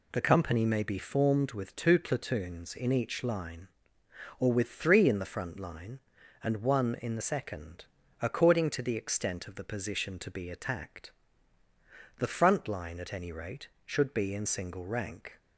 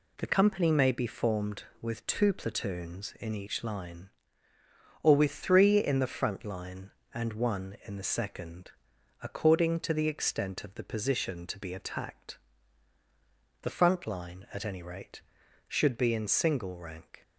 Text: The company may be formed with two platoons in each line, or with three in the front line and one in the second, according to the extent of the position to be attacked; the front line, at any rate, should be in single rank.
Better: neither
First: none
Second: none

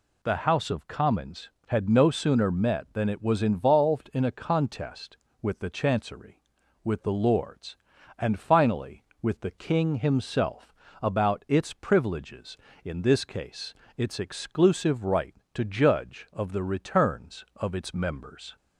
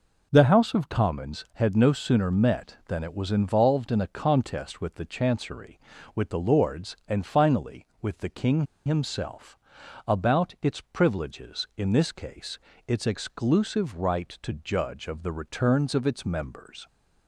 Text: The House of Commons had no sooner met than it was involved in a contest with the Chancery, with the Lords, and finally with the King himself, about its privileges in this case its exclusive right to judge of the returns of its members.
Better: first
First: pauses between "case" and "its"; slight; at 13.7 s; 0.24 s long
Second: pauses between "King" and "himself"; slight; at 8.6 s; 0.21 s long // pauses between "case" and "its"; slight; at 12.5 s; 0.30 s long

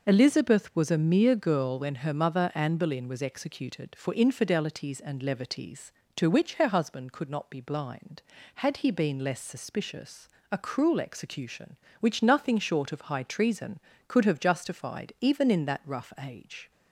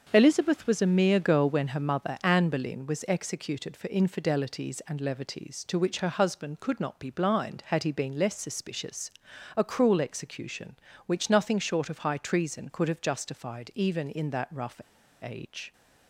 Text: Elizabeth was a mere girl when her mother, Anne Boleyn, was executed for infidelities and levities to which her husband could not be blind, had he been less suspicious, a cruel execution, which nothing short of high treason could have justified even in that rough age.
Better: first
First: none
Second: starts louder than the rest; until 1.1 s; 6.5 dB // pauses between "rough" and "age"; at 14.7 s; 0.41 s long

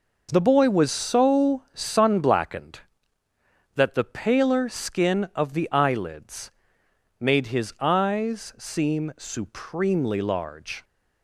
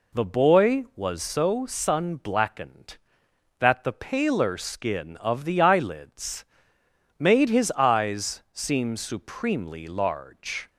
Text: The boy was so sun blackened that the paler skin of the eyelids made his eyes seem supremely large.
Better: neither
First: pauses between "eyelids" and "made"; noticeable; at 6.5 s; 0.68 s long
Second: pauses between "eyelids" and "made"; noticeable; at 6.4 s; 0.72 s long

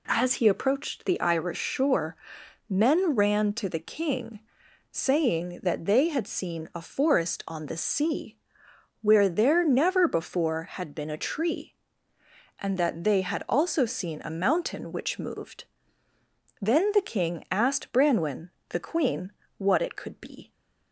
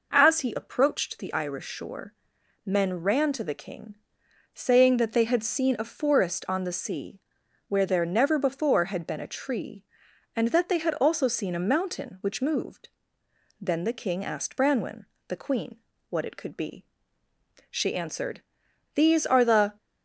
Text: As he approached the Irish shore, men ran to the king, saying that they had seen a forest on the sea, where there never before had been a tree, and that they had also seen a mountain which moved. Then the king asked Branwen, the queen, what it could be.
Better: first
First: none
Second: goes on to say "She answered These are the"; strong; from 17.7 s on; 2.0 s long

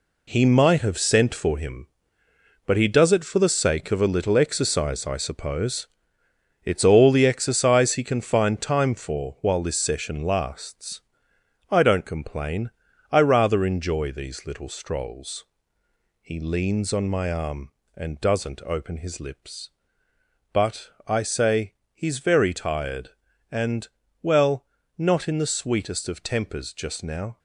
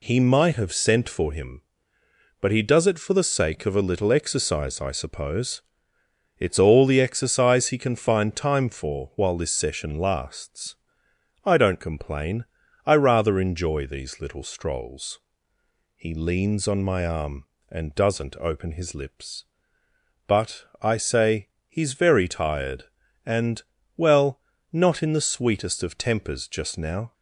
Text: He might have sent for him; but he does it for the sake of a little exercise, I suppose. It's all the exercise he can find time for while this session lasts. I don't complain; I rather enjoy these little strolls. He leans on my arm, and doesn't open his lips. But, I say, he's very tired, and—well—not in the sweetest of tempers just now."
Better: second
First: gets quieter; strong; throughout; 9 dB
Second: none

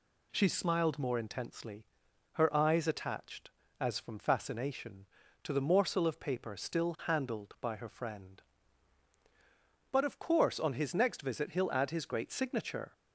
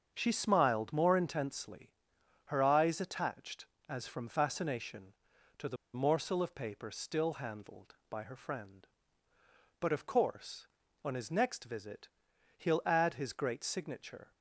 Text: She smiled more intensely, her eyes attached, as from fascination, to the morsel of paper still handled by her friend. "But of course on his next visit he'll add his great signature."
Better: first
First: none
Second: starts louder than the rest; strong; until 1.1 s; 7 dB // pauses between "the" and "morsel"; slight; at 5.7 s; 0.19 s long // pauses between "visit" and "he'll"; noticeable; at 12.0 s; 0.50 s long

